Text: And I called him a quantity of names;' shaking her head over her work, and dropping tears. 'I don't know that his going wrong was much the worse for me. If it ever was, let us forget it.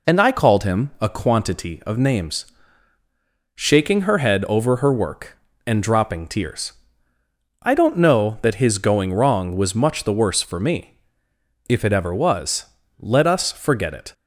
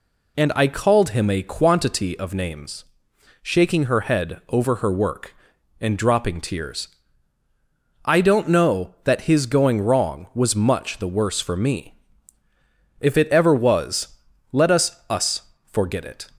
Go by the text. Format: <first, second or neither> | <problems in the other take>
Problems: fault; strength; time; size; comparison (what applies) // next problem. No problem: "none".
first | says "us" twice; at 15.0 s